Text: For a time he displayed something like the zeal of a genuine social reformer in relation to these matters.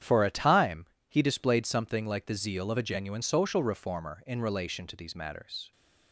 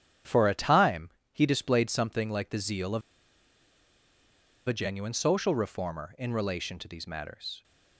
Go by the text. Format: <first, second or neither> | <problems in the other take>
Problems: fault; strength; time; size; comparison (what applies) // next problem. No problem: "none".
first | starts louder than the rest; strong; until 1.4 s; 9 dB; strong in the first // pauses between "time" and "he"; slight; at 1.0 s; 0.22 s long; slight in the first // pauses between "of" and "a"; strong; at 3.0 s; 1.6 s long